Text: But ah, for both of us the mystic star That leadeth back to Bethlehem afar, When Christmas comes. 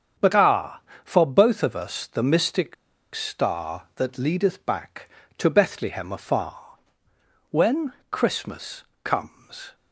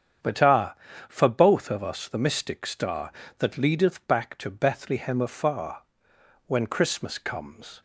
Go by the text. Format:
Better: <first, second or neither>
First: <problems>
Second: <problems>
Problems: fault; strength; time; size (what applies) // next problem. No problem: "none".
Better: second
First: starts louder than the rest; strong; until 1.4 s; 7.5 dB // pauses between "mystic" and "star"; at 2.7 s; 0.40 s long // pauses between "When" and "Christmas"; slight; at 7.9 s; 0.18 s long // pauses between "Christmas" and "comes"; slight; at 8.8 s; 0.20 s long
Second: starts louder than the rest; strong; until 1.5 s; 8 dB